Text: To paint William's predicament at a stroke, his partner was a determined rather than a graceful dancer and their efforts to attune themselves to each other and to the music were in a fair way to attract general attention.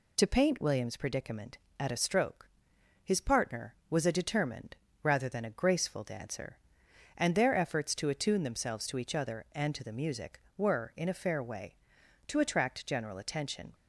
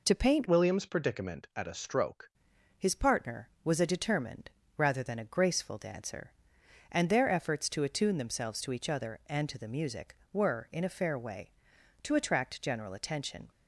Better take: first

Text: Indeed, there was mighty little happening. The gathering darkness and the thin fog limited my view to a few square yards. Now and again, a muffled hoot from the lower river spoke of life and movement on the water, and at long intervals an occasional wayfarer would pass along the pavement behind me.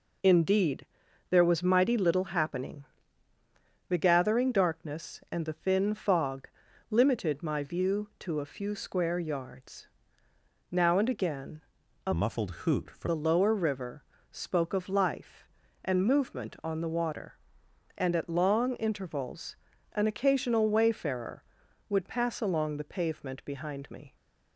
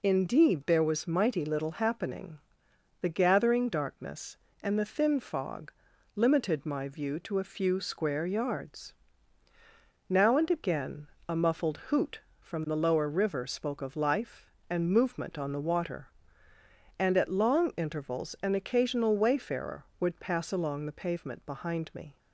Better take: second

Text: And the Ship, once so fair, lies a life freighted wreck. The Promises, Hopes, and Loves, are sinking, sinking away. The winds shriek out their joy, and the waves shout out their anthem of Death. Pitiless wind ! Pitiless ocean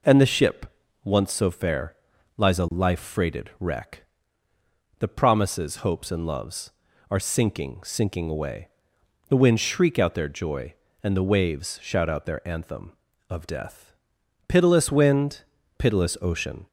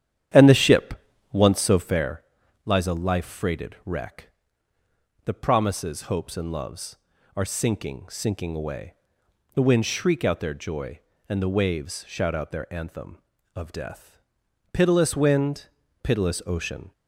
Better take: first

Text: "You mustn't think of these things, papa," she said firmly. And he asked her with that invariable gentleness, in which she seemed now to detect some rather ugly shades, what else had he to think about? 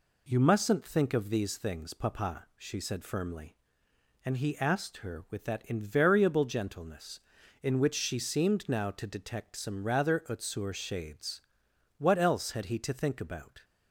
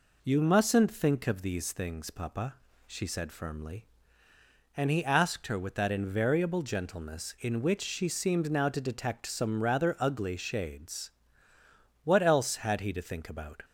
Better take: second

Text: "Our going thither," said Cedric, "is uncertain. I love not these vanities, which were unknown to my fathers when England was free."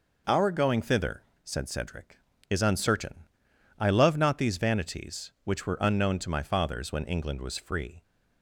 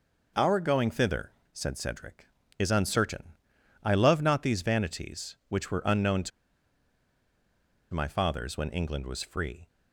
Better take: first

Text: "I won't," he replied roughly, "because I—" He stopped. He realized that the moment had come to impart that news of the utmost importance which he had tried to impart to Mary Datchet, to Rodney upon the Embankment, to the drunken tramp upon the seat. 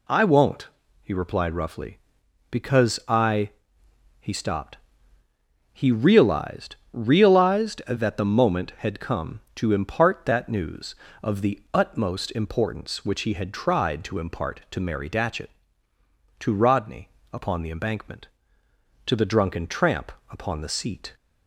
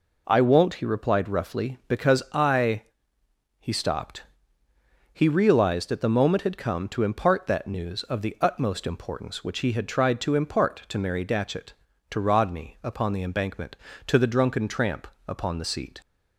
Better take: second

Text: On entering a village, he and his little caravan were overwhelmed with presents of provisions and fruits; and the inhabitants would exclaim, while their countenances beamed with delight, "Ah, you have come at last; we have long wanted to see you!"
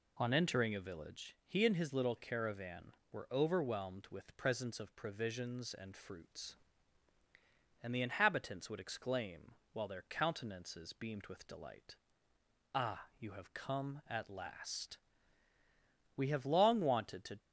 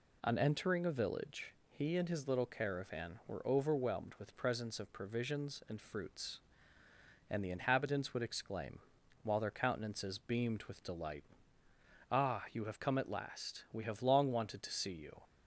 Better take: second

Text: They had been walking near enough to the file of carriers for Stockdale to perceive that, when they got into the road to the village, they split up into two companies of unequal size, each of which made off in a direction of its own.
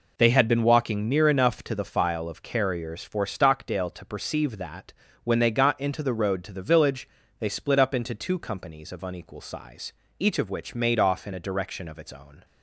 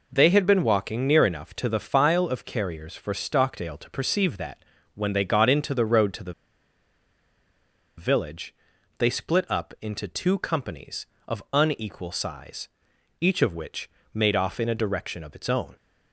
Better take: first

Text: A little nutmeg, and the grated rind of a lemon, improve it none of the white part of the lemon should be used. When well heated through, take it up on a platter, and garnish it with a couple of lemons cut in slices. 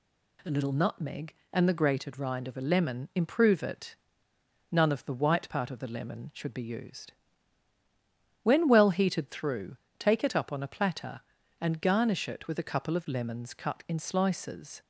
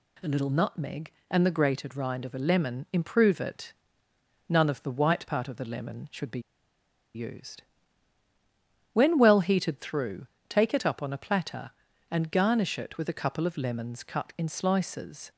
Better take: first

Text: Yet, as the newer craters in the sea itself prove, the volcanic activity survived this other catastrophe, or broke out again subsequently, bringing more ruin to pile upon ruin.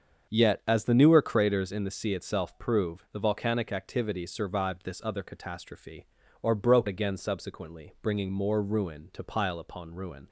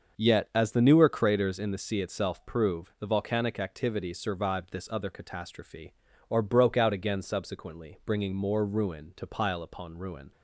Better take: second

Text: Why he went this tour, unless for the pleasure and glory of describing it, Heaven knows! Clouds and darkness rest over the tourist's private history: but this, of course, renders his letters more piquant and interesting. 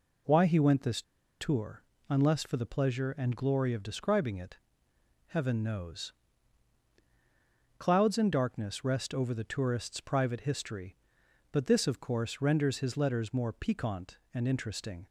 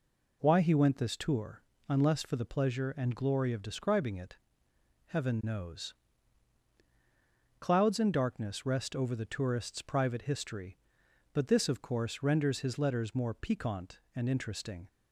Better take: second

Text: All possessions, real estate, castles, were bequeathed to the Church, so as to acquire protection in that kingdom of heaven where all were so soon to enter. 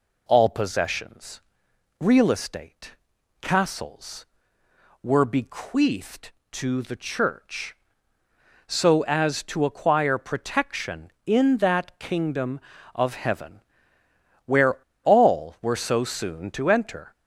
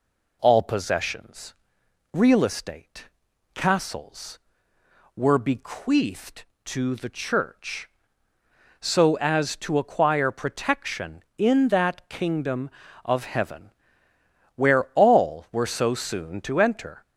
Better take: second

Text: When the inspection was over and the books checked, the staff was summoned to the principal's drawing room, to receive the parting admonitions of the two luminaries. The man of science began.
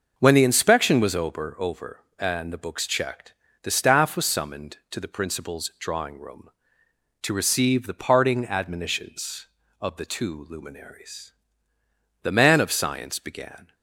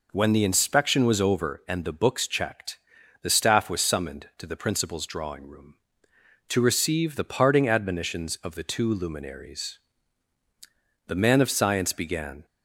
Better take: second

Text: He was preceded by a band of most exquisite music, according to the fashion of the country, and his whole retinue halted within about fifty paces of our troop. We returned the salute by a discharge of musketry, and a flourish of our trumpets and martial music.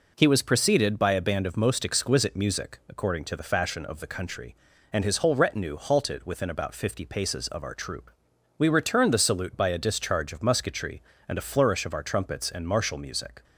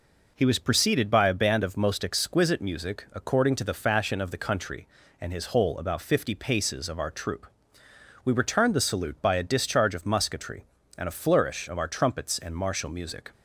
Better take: first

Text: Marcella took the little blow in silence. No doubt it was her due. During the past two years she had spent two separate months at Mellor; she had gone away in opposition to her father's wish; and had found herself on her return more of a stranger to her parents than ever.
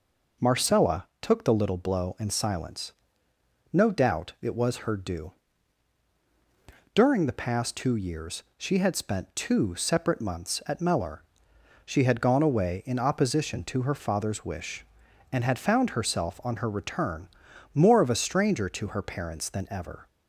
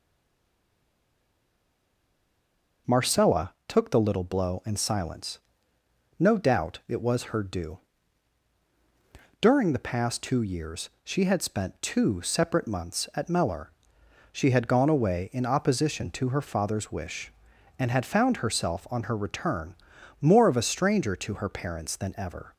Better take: first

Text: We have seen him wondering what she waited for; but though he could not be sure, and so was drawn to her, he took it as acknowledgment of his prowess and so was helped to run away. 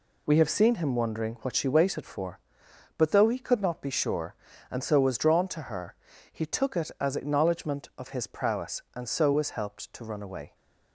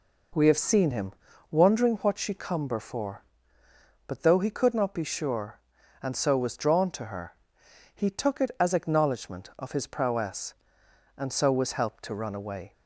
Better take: first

